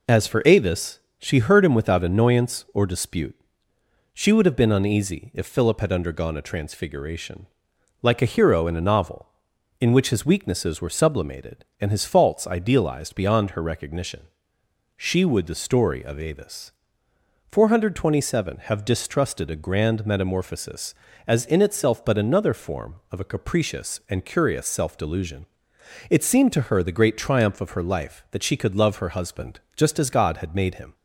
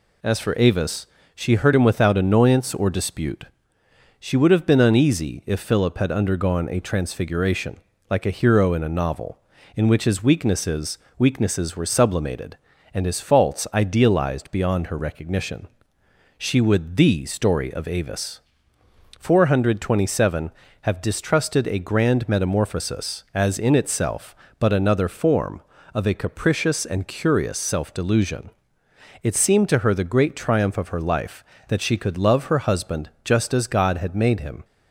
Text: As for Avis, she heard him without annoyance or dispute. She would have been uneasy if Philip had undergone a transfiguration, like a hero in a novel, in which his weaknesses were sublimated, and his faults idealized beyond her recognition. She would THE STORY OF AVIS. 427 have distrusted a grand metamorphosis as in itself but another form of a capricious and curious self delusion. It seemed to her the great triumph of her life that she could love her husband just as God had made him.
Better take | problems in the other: first | says "weaknesses" twice; at 11.1 s // pauses between "husband" and "just"; slight; at 33.0 s; 0.16 s long; slight in the first

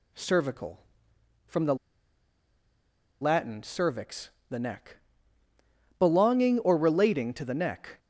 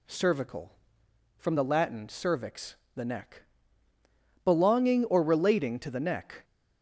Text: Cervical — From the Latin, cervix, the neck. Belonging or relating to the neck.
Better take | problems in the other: second | pauses between "the" and "Latin"; strong; at 1.7 s; 1.4 s long

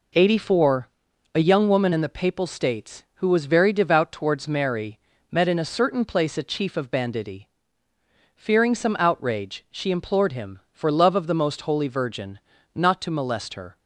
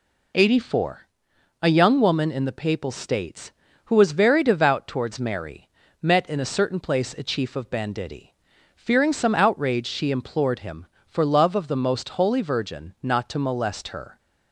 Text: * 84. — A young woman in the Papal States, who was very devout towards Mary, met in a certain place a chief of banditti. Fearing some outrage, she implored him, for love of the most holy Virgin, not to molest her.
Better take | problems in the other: neither | none

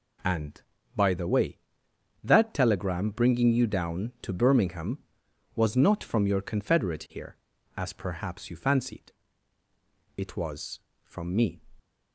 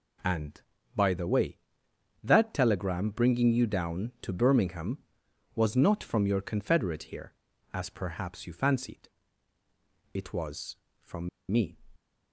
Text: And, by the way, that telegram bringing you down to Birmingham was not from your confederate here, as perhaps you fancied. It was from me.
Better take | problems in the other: first | pauses between "from" and "me"; slight; at 11.2 s; 0.21 s long

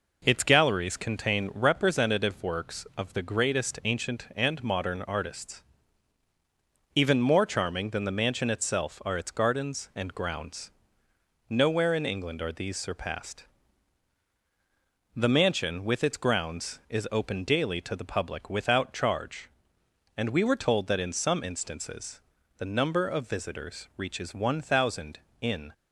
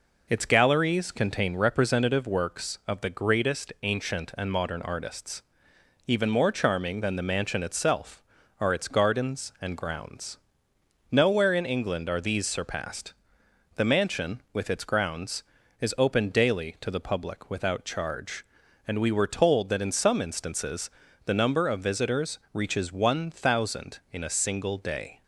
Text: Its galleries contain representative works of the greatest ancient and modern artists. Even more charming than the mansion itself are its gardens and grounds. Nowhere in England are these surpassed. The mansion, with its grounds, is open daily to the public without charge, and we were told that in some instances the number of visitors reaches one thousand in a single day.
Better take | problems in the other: second | pauses between "instances" and "the"; at 22.1 s; 0.38 s long; slight in the second // stops before "a single day"; at 25.7 s

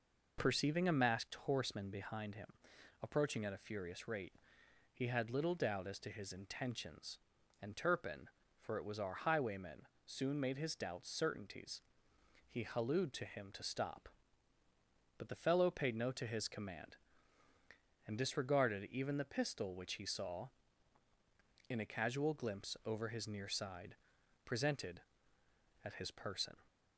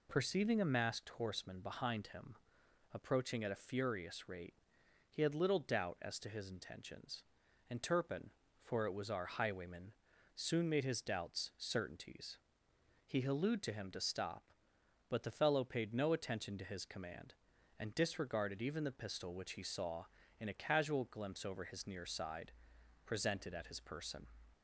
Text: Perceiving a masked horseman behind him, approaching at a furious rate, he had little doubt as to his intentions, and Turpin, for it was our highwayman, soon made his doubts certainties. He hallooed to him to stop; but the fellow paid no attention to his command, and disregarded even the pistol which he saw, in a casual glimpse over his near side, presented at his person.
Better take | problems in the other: second | skips "attention"; at 16.1 s

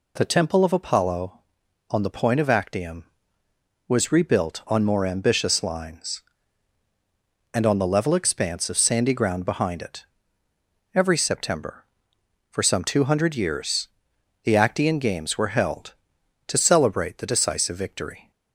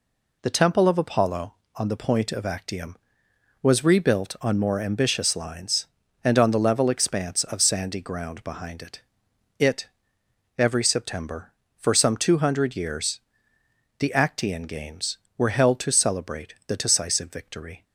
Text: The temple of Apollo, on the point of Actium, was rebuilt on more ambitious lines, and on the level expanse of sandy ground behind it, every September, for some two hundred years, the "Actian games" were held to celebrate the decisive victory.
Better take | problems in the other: first | says "it" twice; at 9.5 s

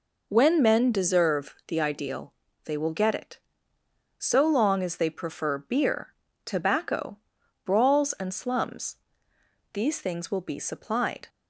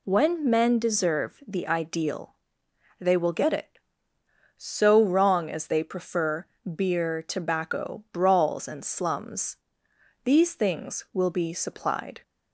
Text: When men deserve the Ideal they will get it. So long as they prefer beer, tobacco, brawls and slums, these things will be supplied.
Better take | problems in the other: first | pauses between "Ideal" and "they"; noticeable; at 2.3 s; 0.66 s long; slight in the first // says "wrong" for "long"; at 5.0 s // pauses between "prefer" and "beer"; slight; at 6.4 s; 0.30 s long

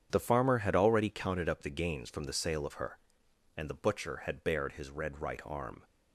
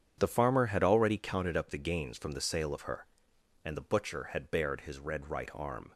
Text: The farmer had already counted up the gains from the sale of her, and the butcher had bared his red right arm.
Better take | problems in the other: neither | starts louder than the rest; strong; the same in both

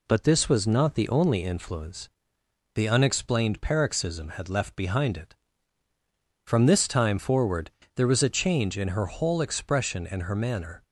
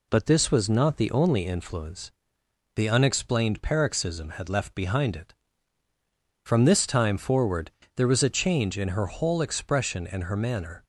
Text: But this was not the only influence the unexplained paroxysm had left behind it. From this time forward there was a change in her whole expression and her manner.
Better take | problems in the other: neither | pauses between "influence" and "the"; noticeable; the same in both // pauses between "forward" and "there"; slight; the same in both

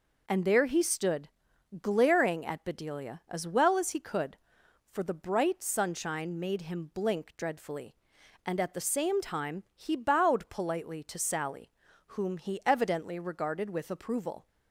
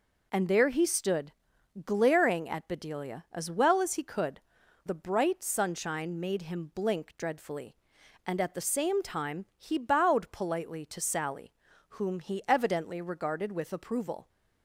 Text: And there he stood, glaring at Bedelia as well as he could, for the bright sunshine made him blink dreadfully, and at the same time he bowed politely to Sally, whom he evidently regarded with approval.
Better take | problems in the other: first | skips "for"; at 4.6 s

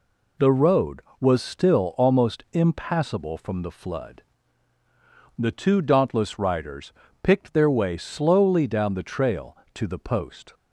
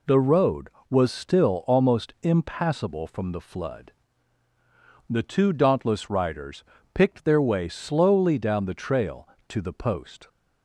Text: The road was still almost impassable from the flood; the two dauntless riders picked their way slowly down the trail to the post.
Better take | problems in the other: neither | pauses between "riders" and "picked"; slight; the same in both

